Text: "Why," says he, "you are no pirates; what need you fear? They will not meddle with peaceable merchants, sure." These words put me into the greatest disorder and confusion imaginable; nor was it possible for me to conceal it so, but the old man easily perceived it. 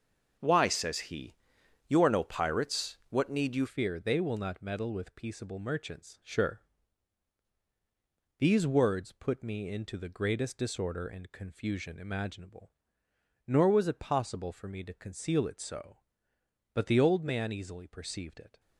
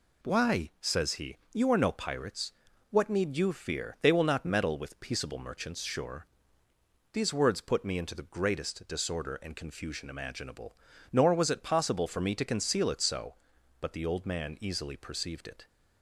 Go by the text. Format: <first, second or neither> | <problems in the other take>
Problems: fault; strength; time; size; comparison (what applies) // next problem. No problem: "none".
second | starts louder than the rest; until 1.9 s; 6.5 dB // changes voice at "fear"; from 3.6 s on; 14.9 s long